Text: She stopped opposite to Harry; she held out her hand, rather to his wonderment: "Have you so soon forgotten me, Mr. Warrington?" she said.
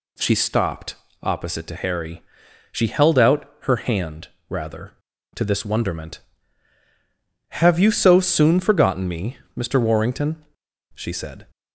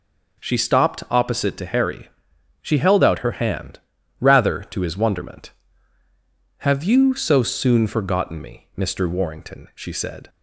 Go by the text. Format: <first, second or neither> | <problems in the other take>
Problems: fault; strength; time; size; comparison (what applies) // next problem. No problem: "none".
second | pauses between "stopped" and "opposite"; slight; at 0.9 s; 0.28 s long // says "this" for "his"; at 5.4 s